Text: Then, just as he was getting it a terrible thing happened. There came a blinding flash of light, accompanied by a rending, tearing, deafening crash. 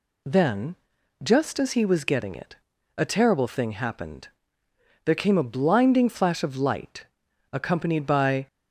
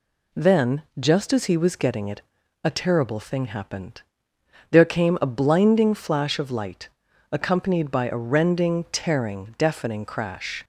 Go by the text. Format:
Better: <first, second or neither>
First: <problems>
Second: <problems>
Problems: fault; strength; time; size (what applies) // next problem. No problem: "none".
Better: second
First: pauses between "it" and "a"; at 2.5 s; 0.42 s long // stops before "a rending tearing deafening crash"; at 8.4 s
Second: pauses between "it" and "a"; at 2.2 s; 0.42 s long